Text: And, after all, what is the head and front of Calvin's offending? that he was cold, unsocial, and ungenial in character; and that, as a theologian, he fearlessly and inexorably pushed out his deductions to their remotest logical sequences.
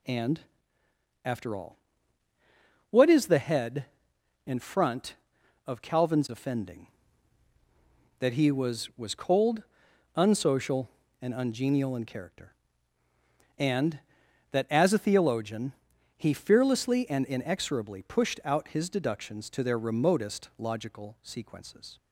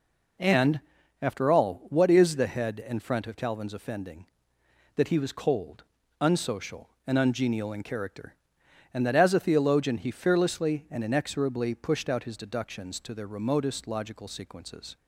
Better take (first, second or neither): second